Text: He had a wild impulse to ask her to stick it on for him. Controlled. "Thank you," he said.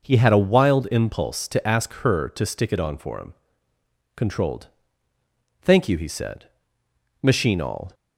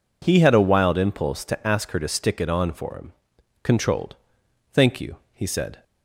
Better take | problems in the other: second | goes on to say "Machine all"; noticeable; from 7.2 s on; 0.72 s long

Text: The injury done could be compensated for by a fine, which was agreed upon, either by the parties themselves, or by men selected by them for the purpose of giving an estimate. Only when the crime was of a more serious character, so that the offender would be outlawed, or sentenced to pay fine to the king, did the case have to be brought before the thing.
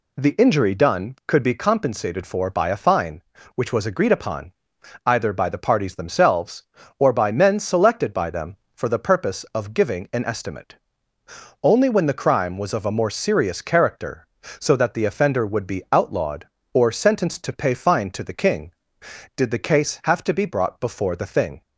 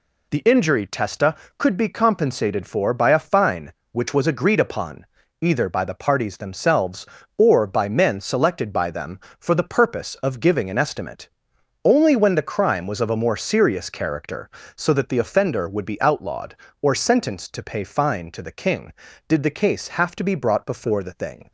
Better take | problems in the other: first | says "testa" for "done"; at 0.8 s

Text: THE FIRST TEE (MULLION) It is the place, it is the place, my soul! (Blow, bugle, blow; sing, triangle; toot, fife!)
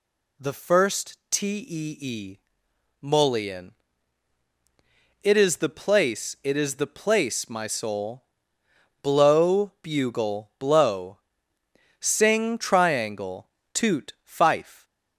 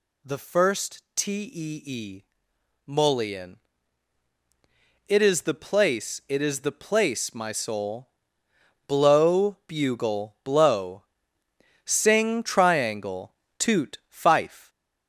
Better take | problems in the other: first | gets louder; slight; throughout; 3 dB

